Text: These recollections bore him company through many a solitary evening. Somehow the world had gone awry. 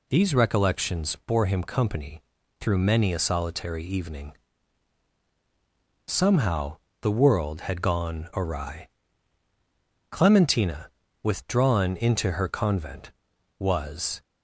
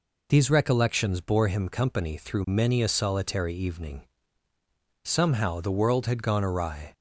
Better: second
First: pauses between "company" and "through"; at 2.2 s; 0.40 s long // pauses between "Somehow" and "the"; slight; at 6.7 s; 0.24 s long // goes on to say "Clementina withdrawn into her convent was"; strong; from 10.1 s on; 4.1 s long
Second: none

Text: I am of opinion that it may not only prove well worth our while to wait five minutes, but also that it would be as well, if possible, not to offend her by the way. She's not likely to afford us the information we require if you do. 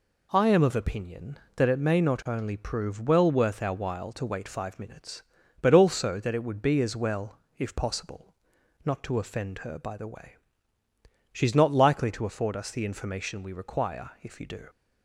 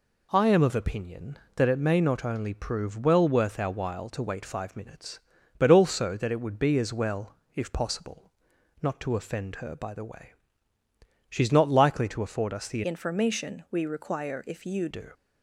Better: first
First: none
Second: changes voice from "information" to "you"; from 12.8 to 14.8 s; 2.0 s long

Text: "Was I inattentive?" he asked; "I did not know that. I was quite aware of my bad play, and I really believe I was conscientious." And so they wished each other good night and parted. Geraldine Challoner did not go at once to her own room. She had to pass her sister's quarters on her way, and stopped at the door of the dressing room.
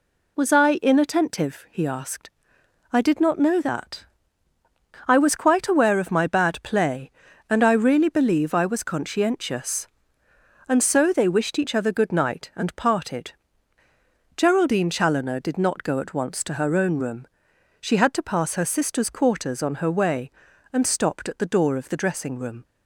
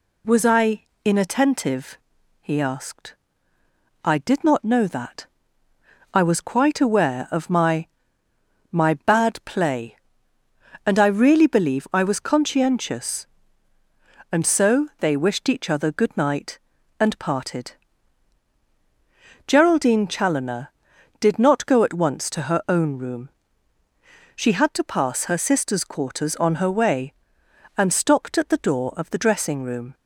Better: first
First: none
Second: pauses between "I" and "inattentive"; slight; at 0.8 s; 0.22 s long // says "my" twice; at 8.7 s

